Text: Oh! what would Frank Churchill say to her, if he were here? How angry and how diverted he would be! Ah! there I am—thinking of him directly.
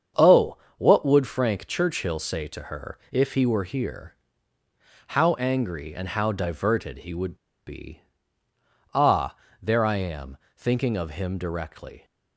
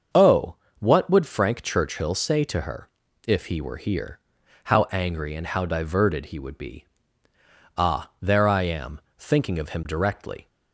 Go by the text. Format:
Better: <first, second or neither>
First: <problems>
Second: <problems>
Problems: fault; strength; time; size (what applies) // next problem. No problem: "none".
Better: second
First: starts louder than the rest; strong; until 1.3 s; 7.5 dB // pauses between "would" and "be"; slight; at 7.3 s; 0.32 s long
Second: starts louder than the rest; until 1.3 s; 6.5 dB